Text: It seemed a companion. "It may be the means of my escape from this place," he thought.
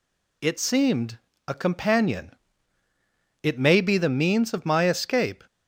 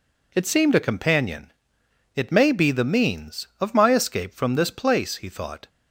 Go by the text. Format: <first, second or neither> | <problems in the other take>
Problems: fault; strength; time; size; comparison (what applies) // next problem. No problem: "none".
second | pauses between "seemed" and "a"; slight; at 1.1 s; 0.30 s long // stops before "from this place he thought"; at 5.4 s